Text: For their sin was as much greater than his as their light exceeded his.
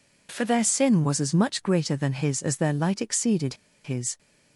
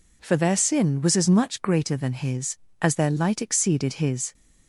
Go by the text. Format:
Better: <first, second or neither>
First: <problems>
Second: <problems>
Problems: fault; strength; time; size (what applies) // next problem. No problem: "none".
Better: second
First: pauses between "exceeded" and "his"; slight; at 3.5 s; 0.30 s long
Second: none